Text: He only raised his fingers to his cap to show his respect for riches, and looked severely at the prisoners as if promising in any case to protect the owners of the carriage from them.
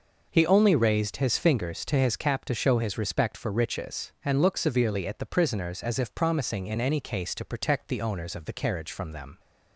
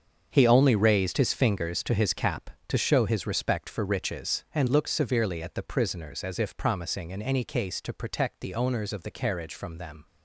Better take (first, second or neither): first